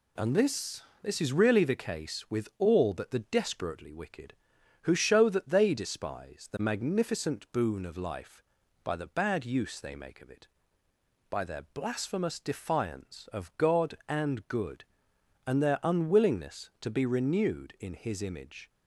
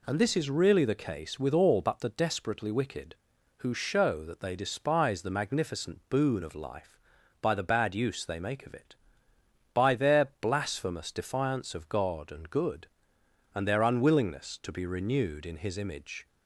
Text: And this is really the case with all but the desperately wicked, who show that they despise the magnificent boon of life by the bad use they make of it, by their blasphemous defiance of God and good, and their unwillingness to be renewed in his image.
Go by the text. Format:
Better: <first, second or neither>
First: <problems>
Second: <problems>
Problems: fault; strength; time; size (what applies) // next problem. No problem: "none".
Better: second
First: says "this" twice; at 1.0 s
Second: none